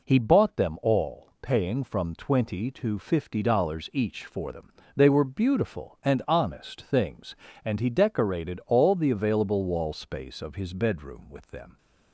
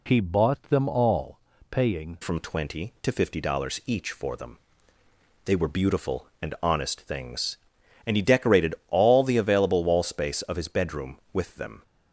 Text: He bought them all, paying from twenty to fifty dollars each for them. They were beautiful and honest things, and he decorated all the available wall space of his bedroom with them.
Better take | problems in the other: first | changes voice at "from"; from 2.2 s on; 9.6 s long

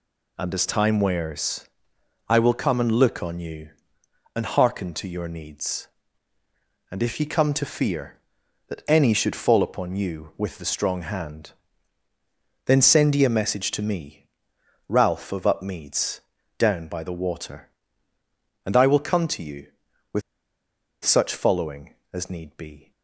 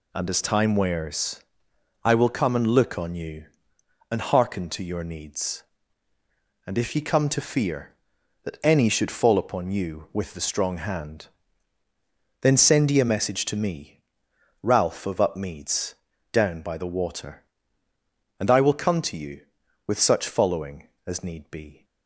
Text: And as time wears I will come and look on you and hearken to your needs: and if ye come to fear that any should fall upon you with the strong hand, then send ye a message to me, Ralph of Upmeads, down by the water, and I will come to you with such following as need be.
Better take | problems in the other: second | pauses between "wears" and "I"; noticeable; at 1.6 s; 0.60 s long; noticeable in the second // pauses between "with" and "such"; noticeable; at 20.2 s; 0.83 s long

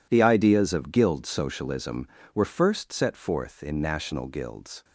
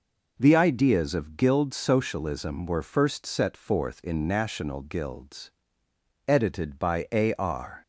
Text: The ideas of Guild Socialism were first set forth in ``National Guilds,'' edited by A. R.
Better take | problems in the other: second | stops before "edited by A R"; at 4.8 s

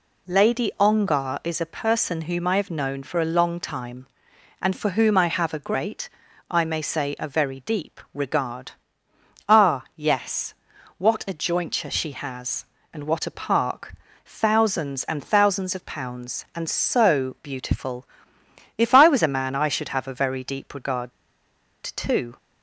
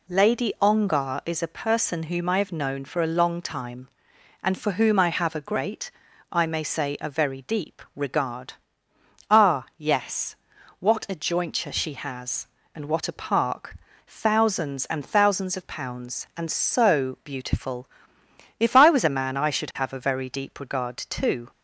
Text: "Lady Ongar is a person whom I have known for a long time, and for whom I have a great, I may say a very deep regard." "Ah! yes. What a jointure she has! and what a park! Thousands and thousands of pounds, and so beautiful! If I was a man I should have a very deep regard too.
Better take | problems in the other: second | pauses between "regard" and "too"; noticeable; at 21.1 s; 0.72 s long

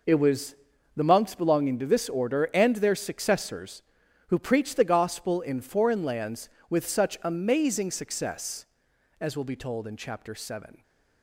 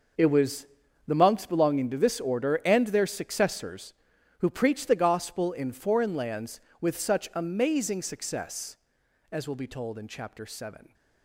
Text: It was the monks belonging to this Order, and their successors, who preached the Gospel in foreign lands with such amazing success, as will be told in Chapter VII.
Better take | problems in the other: first | gets quieter; strong; throughout; 13.5 dB // pauses between "was" and "the"; at 0.6 s; 0.42 s long; also in the first

